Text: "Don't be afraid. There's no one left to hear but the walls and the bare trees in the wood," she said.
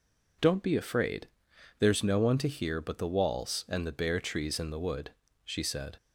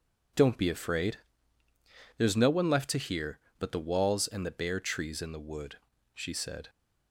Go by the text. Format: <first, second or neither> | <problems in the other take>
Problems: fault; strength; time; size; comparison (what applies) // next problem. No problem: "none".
second | skips "left"; at 2.3 s